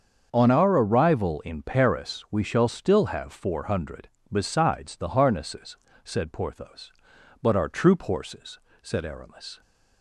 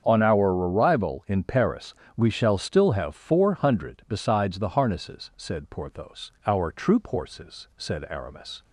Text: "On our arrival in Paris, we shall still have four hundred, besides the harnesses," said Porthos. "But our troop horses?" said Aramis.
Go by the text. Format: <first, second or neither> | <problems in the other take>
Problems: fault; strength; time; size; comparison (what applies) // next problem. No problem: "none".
first | starts louder than the rest; strong; until 1.0 s; 7.5 dB; also in the first // skips "But"; at 6.3 s